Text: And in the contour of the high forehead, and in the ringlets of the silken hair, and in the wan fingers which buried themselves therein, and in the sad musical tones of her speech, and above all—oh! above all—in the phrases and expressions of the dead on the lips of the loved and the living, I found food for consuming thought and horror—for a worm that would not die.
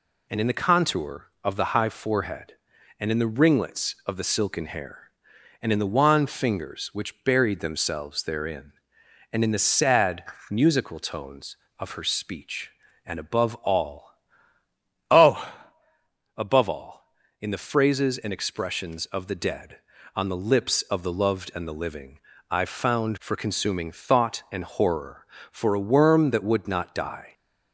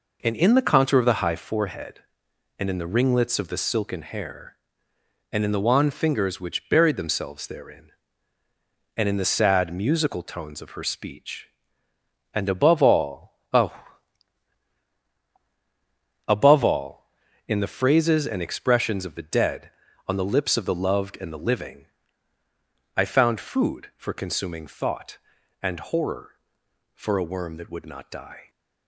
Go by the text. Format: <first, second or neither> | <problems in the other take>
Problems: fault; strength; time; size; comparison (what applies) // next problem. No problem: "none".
second | pauses between "sad" and "musical"; slight; at 10.2 s; 0.26 s long // skips "food"; at 23.1 s